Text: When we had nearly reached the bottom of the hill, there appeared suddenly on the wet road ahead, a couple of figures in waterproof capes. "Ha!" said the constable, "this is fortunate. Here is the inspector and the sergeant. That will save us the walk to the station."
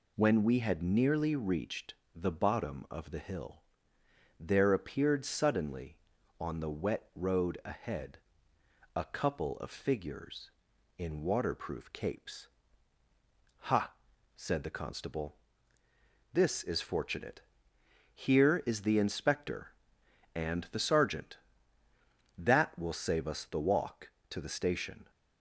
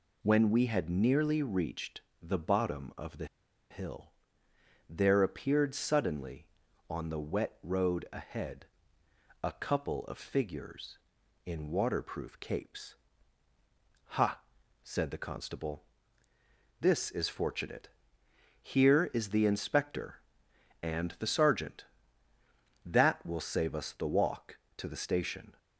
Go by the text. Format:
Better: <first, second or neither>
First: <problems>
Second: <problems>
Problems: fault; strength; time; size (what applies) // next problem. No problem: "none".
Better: first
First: pauses between "reached" and "the"; slight; at 1.9 s; 0.20 s long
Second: pauses between "reached" and "the"; slight; at 2.0 s; 0.20 s long // pauses between "the" and "hill"; at 3.2 s; 0.45 s long